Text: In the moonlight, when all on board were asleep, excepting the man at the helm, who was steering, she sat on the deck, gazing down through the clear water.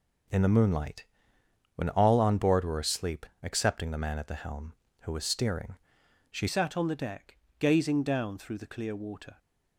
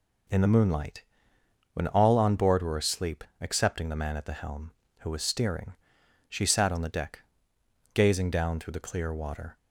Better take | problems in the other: second | changes voice at "sat"; from 6.4 s on; 2.9 s long

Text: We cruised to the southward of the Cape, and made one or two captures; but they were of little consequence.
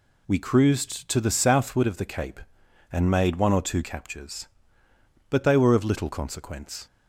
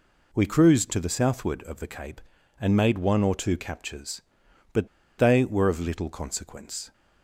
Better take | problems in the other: first | pauses between "but" and "they"; slight; at 4.8 s; 0.30 s long

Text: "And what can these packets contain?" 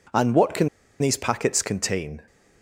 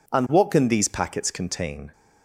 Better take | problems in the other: second | pauses between "can" and "these"; slight; at 0.6 s; 0.32 s long

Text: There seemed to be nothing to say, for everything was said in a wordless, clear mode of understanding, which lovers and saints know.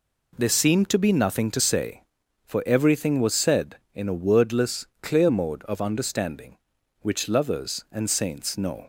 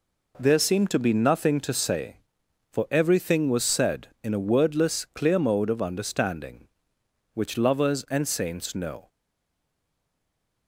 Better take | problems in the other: first | stays silent after the last word; noticeable; from 9.0 s on; 1.6 s long

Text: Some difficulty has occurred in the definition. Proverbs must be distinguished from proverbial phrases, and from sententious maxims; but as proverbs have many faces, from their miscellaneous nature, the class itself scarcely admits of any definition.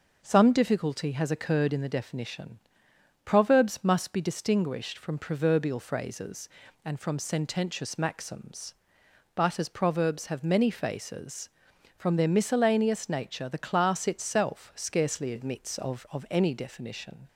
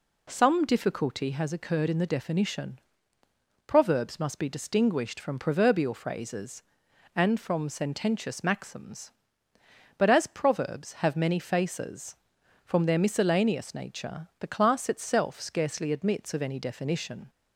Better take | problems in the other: second | says "of" twice; at 16.1 s

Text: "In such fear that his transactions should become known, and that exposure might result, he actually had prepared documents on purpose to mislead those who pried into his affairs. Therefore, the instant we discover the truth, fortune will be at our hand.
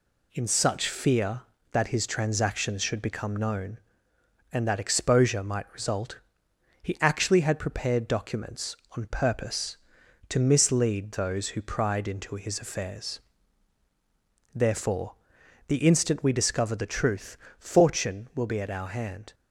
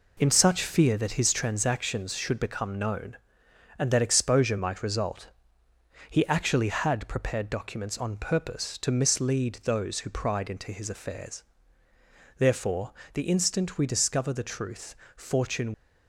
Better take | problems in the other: first | stops before "will be at our hand"; at 15.7 s

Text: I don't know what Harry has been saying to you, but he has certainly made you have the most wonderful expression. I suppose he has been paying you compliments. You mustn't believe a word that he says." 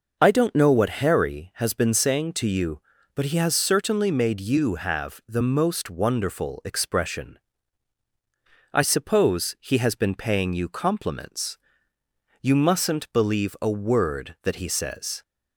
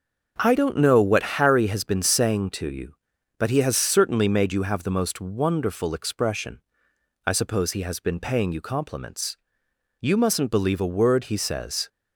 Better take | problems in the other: first | starts louder than the rest; until 1.3 s; 6.5 dB // skips "that"; at 11.2 s

